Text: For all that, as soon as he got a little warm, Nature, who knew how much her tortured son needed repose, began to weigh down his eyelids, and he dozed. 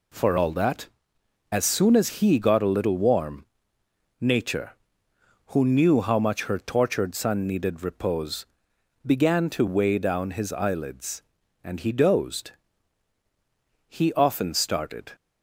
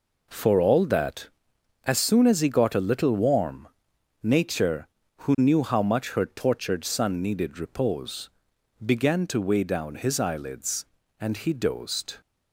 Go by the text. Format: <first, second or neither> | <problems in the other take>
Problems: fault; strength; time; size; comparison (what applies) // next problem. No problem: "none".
second | goes on to say "He often started"; noticeable; from 13.8 s on; 1.2 s long